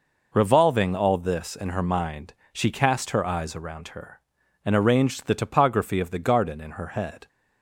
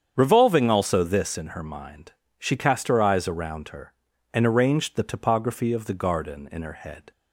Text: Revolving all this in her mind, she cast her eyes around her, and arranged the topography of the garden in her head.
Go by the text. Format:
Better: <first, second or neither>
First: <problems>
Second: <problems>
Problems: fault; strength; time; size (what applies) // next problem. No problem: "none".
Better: first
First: none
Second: starts louder than the rest; strong; until 1.1 s; 8 dB // says "also" for "all"; at 0.6 s